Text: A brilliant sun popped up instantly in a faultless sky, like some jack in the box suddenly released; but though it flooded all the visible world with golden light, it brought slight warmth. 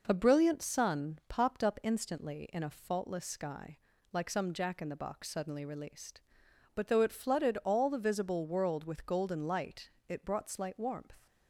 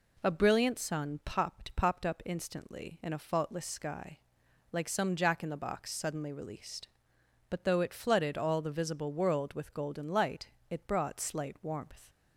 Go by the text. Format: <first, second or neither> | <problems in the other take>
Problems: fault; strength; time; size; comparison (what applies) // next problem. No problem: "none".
first | says "popped" twice; at 1.7 s